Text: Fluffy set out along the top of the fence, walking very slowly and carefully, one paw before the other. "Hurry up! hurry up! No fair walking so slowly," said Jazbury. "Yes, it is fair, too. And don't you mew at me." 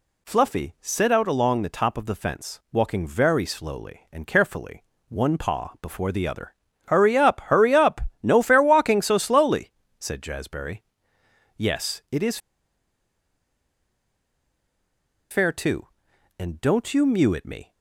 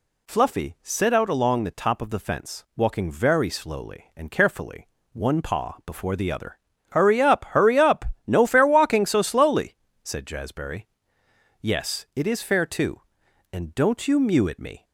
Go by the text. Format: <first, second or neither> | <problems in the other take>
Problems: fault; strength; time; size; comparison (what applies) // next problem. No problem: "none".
second | pauses between "is" and "fair"; strong; at 12.3 s; 2.9 s long